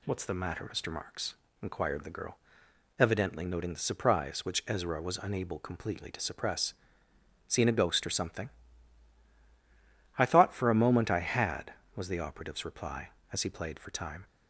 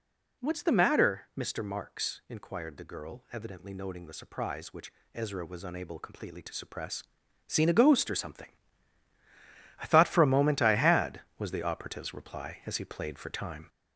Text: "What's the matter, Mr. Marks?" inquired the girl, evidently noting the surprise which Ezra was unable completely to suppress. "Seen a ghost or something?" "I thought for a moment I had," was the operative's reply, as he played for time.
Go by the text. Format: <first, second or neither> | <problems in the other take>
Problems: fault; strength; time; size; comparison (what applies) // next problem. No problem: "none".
first | gets louder; noticeable; throughout; 4 dB // pauses between "which" and "Ezra"; slight; at 4.9 s; 0.22 s long